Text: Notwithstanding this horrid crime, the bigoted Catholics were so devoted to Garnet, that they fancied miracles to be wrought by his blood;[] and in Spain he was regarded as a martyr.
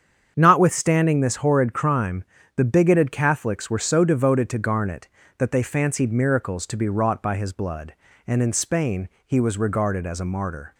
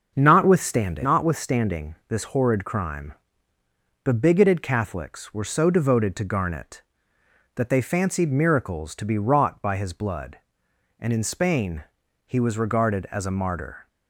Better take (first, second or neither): first